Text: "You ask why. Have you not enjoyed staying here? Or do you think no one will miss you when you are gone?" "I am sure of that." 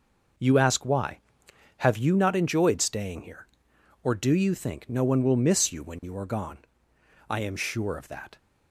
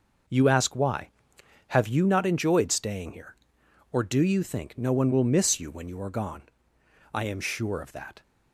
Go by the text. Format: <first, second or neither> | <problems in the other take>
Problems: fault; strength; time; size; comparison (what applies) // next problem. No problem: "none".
neither | none